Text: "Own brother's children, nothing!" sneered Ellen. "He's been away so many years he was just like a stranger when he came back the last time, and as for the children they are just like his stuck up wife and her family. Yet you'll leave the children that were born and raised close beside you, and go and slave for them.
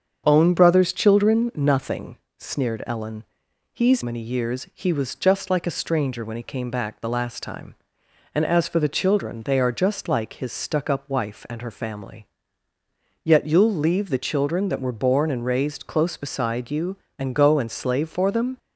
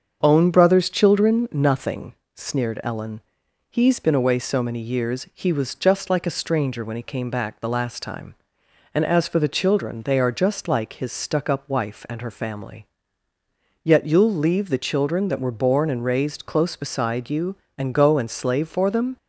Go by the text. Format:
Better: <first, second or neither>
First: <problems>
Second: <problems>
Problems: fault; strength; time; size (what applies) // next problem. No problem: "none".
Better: second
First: starts louder than the rest; until 1.2 s; 7 dB // skips "been away so"; at 4.0 s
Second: starts louder than the rest; until 1.2 s; 7 dB